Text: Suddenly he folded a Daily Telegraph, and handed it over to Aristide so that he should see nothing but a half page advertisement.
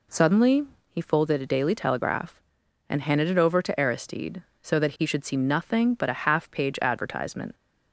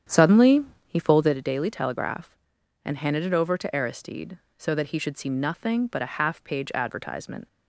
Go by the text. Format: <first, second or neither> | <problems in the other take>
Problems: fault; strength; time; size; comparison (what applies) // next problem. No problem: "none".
first | starts louder than the rest; strong; until 1.4 s; 9 dB // pauses between "Suddenly" and "he"; slight; at 0.6 s; 0.22 s long; slight in the first